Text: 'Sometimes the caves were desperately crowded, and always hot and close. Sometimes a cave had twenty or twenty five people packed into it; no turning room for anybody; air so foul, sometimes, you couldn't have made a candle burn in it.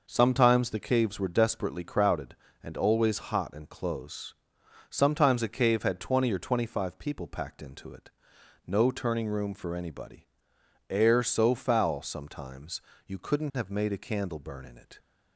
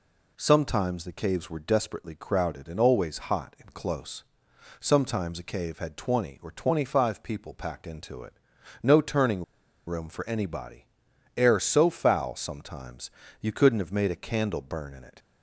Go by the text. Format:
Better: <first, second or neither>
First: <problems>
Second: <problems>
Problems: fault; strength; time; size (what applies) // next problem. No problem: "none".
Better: first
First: none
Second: pauses between "turning" and "room"; at 9.4 s; 0.43 s long